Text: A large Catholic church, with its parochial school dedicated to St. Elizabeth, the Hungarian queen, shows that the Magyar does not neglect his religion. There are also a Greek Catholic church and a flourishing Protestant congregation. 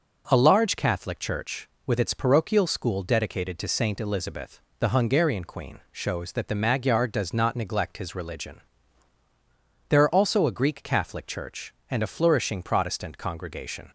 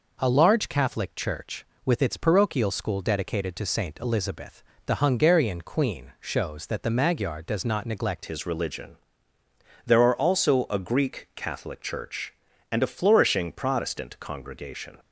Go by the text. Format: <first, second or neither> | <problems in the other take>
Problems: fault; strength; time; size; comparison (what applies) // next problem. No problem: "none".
first | changes voice at "his"; from 8.2 s on; 6.7 s long